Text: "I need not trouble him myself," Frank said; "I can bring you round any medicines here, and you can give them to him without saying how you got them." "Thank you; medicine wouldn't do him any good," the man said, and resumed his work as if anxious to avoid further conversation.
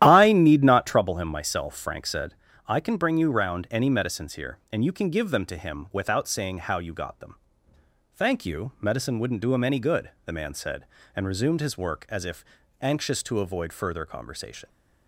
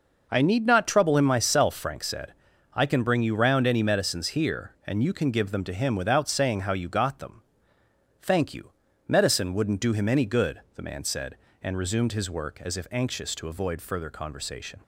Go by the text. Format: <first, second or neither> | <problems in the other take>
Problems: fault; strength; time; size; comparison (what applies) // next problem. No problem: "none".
second | starts louder than the rest; strong; until 1.1 s; 12 dB // pauses between "if" and "anxious"; slight; at 12.4 s; 0.36 s long